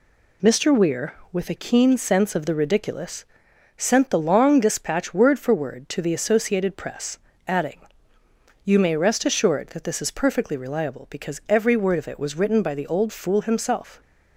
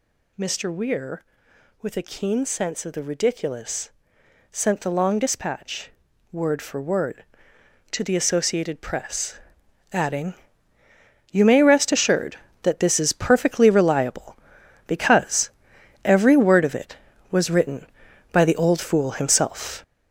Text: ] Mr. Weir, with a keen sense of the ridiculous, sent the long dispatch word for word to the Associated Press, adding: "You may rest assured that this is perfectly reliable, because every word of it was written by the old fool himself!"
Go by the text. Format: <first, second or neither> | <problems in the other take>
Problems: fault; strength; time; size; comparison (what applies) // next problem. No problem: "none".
first | gets louder; throughout; 6.5 dB // pauses between "dispatch" and "word"; at 5.9 s; 0.40 s long // pauses between "because" and "every"; noticeable; at 15.5 s; 0.54 s long